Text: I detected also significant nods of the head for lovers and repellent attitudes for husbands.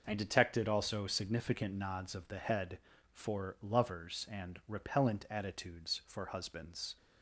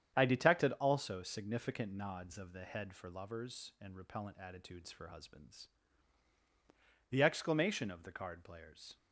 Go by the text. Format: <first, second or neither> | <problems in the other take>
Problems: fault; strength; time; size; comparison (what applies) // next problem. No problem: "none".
first | starts louder than the rest; strong; until 1.1 s; 9 dB // goes on to say "The exclamation of the card players"; strong; from 7.0 s on; 1.8 s long